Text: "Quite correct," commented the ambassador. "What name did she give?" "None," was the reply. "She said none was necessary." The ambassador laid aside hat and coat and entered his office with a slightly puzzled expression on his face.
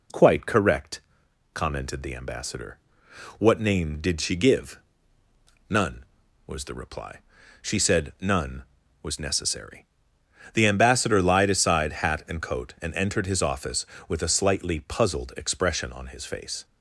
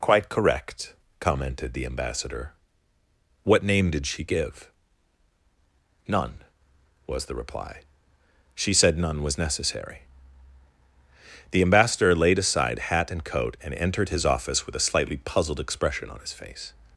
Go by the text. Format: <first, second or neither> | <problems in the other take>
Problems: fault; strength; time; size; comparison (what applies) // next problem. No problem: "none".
second | says "lied" for "laid"; at 11.2 s